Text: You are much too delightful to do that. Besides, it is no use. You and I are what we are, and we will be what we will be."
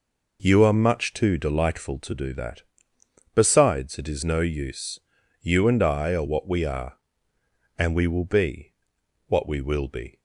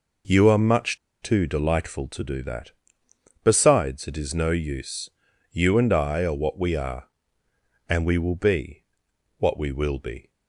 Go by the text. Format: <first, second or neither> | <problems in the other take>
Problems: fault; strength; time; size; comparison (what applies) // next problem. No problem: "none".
first | pauses between "much" and "too"; slight; at 0.9 s; 0.24 s long // pauses between "be" and "what"; noticeable; at 8.8 s; 0.56 s long; noticeable in the first